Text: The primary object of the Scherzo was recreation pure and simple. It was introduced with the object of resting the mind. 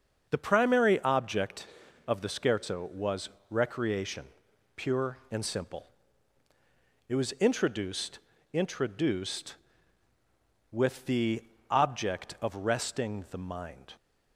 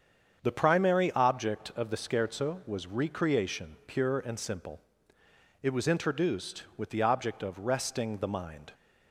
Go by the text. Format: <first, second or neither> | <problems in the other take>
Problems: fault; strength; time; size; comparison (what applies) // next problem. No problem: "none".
second | starts louder than the rest; until 1.3 s; 6.5 dB; strong in the second // pauses between "was" and "recreation"; slight; at 3.2 s; 0.20 s long // pauses between "recreation" and "pure"; noticeable; at 4.2 s; 0.50 s long // says "introduced" twice; at 8.5 s // pauses between "the" and "object"; slight; at 11.4 s; 0.28 s long